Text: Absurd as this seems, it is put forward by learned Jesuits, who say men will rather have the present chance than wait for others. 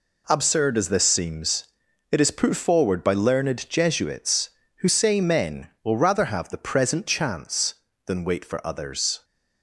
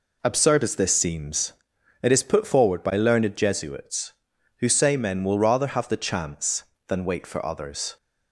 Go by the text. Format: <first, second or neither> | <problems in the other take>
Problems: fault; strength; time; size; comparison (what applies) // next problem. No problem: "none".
first | skips "present"; at 5.9 s